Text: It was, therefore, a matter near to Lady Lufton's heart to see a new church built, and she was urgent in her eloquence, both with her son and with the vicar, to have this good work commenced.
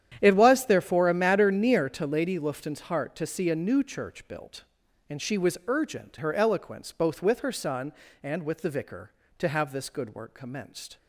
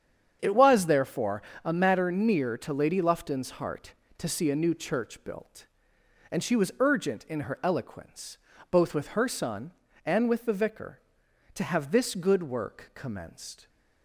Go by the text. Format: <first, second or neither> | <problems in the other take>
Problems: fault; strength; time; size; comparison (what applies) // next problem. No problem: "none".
second | starts louder than the rest; strong; until 1.2 s; 10 dB; strong in the second // skips "in"; at 6.1 s